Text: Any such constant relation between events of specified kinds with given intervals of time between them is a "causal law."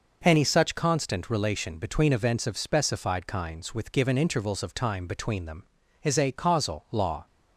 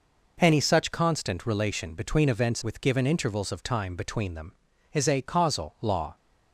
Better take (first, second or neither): first